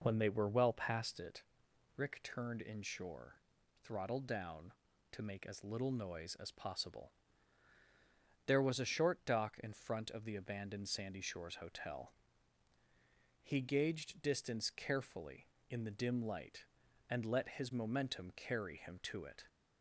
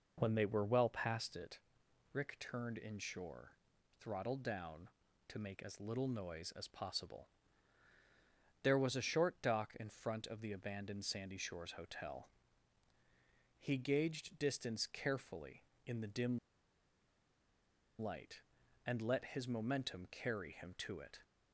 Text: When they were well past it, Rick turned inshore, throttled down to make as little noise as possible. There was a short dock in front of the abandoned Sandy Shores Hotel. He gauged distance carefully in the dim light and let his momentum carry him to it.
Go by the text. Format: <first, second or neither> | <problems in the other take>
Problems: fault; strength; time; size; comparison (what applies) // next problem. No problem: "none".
first | pauses between "dim" and "light"; strong; at 16.3 s; 1.6 s long